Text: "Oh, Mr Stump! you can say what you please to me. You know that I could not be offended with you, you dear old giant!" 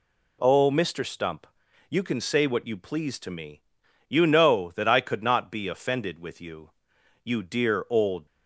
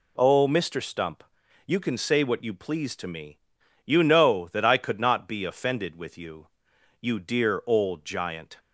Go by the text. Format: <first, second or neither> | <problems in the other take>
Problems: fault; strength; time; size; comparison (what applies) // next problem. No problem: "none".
second | stops before "giant"; at 8.2 s